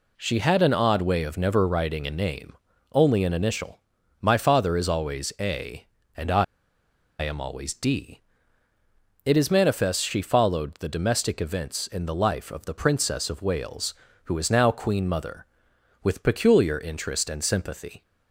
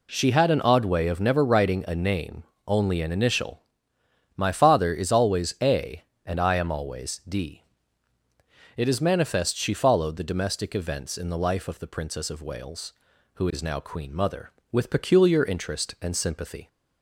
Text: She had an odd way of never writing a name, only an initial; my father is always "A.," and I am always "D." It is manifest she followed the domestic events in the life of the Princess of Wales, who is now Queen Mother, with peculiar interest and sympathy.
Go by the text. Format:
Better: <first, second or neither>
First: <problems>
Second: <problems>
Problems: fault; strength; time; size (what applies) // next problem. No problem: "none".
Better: second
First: pauses between "I" and "am"; noticeable; at 6.4 s; 0.76 s long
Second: none